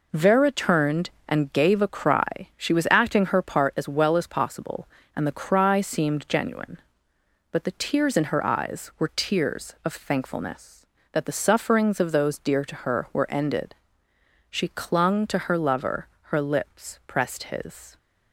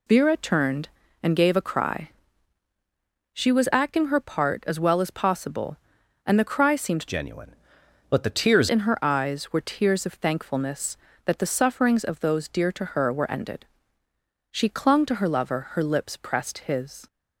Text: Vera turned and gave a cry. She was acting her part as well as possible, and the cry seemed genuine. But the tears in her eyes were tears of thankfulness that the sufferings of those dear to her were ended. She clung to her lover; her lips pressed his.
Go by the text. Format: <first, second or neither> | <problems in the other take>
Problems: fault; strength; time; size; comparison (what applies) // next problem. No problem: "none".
first | changes voice from "genuine" to "tears"; from 7.0 to 8.6 s; 1.6 s long